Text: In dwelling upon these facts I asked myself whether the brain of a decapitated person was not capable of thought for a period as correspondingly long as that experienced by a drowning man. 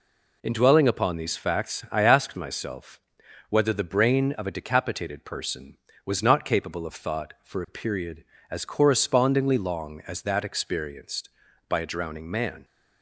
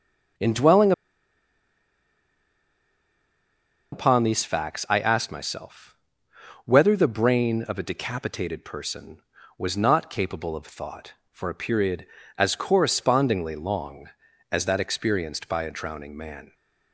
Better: first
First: pauses between "myself" and "whether"; noticeable; at 2.9 s; 0.52 s long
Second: starts louder than the rest; until 4.3 s; 6.5 dB // pauses between "dwelling" and "upon"; strong; at 0.9 s; 3.0 s long // pauses between "myself" and "whether"; noticeable; at 5.9 s; 0.70 s long

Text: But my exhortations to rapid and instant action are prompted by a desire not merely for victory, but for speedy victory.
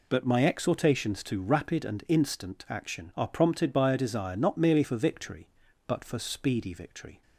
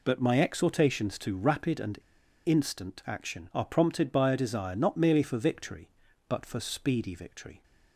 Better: first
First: none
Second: pauses between "and" and "instant"; noticeable; at 1.9 s; 0.46 s long

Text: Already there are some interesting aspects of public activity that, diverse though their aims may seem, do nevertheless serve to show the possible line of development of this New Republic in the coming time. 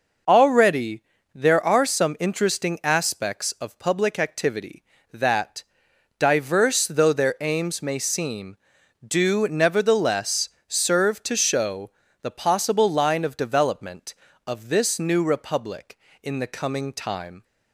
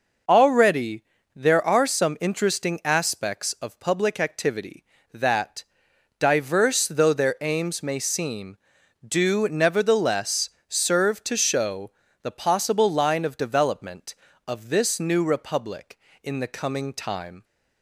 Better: neither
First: pauses between "Already" and "there"; slight; at 1.0 s; 0.32 s long // pauses between "nevertheless" and "serve"; slight; at 10.4 s; 0.18 s long // pauses between "show" and "the"; slight; at 11.9 s; 0.30 s long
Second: pauses between "Already" and "there"; slight; at 1.0 s; 0.32 s long // pauses between "nevertheless" and "serve"; slight; at 10.4 s; 0.18 s long // pauses between "show" and "the"; slight; at 11.9 s; 0.30 s long

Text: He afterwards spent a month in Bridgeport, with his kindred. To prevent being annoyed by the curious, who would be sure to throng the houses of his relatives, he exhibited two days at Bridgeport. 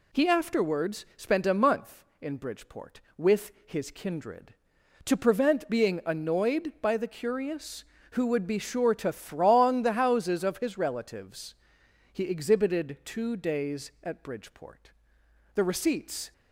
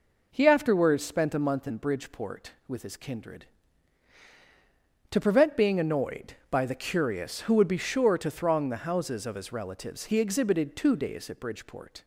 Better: second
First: pauses between "with" and "his"; slight; at 3.5 s; 0.16 s long // goes on to say "The receipts"; noticeable; from 15.5 s on; 0.78 s long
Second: none

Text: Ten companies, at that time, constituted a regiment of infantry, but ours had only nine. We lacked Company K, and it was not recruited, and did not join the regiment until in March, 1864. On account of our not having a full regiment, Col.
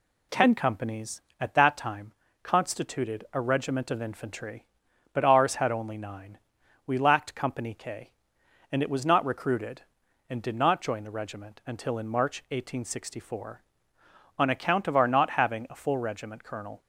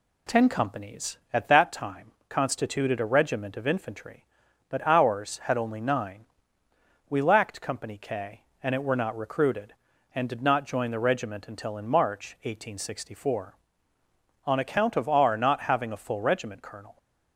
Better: first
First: none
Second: says "were" for "was"; at 8.8 s

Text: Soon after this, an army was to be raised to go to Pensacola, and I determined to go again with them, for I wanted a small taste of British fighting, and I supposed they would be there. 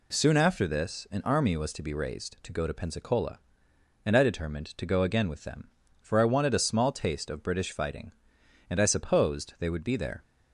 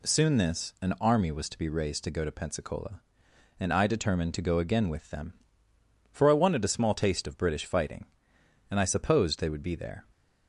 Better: first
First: none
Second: skips "after"; at 0.3 s

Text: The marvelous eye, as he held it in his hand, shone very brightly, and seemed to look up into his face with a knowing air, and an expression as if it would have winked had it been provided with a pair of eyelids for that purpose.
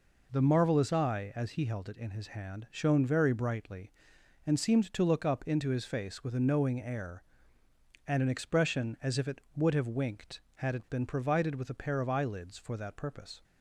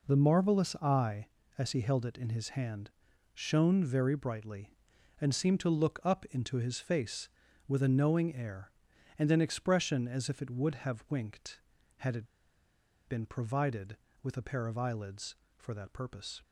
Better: first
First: none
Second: pauses between "it" and "been"; noticeable; at 12.2 s; 0.83 s long

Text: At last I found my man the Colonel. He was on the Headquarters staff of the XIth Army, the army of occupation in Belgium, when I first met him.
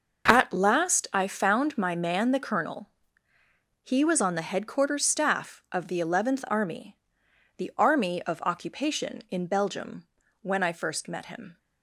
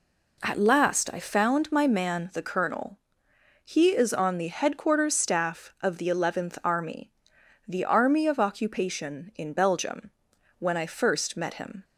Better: first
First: none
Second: says "is" for "was"; at 3.8 s

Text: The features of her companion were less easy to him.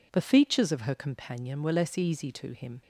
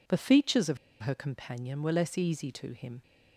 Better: first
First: none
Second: pauses between "of" and "her"; slight; at 0.7 s; 0.24 s long

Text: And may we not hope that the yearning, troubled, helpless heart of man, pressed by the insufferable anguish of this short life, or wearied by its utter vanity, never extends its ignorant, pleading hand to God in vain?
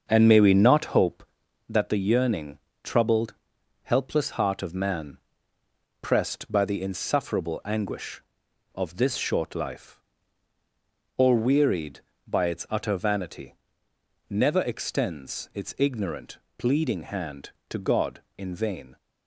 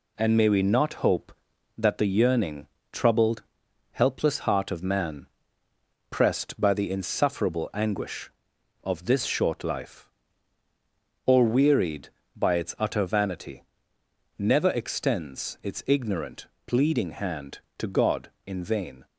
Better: second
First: starts louder than the rest; until 1.1 s; 6.5 dB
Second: none

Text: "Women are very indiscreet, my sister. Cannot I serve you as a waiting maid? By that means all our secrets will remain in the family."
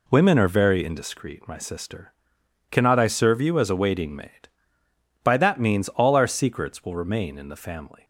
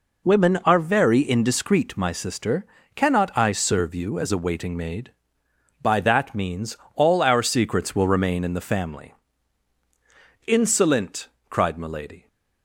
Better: first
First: none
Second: pauses between "means" and "all"; slight; at 6.7 s; 0.18 s long // goes on to say "Insolent cried Milady"; strong; from 10.4 s on; 1.8 s long

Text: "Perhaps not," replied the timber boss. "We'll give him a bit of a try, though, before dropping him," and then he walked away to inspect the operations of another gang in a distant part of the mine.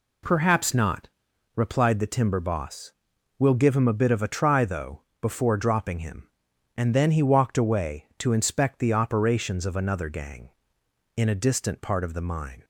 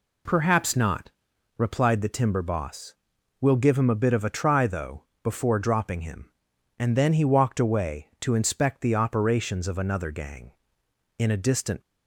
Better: first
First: none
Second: stops before "part of the mine"; at 11.8 s

